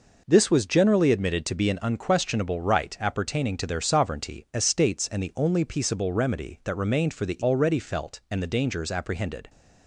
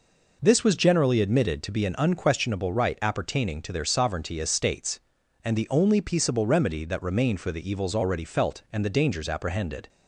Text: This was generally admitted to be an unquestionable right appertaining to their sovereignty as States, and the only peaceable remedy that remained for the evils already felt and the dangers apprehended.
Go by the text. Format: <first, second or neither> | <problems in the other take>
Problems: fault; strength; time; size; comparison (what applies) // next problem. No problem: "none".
second | skips "evils"; at 7.4 s